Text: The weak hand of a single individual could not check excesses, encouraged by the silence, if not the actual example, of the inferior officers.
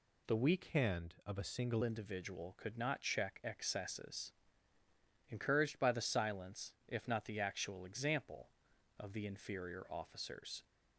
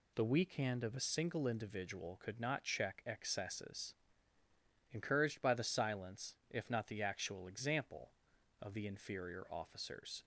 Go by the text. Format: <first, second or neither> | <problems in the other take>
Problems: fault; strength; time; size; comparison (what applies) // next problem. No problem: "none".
second | changes voice from "hand" to "single"; from 0.6 to 1.8 s; 1.2 s long